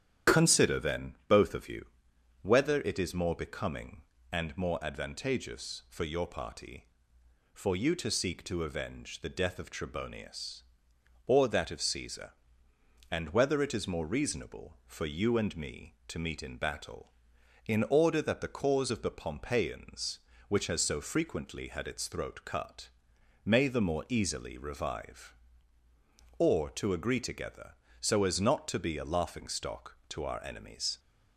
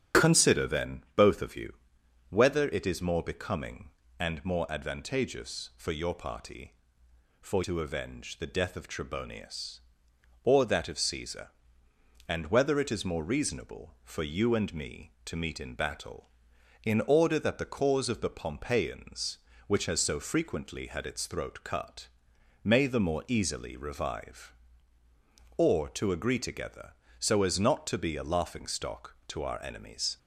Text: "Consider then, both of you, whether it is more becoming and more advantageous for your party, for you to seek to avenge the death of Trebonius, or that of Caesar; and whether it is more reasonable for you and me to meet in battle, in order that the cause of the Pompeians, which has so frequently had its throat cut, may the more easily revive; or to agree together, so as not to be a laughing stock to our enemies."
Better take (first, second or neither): first